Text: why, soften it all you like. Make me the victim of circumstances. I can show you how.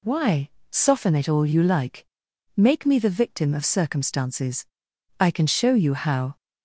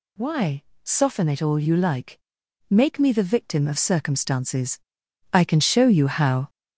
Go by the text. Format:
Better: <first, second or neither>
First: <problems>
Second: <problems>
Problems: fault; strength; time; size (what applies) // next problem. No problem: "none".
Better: first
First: none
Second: gets louder; noticeable; throughout; 6 dB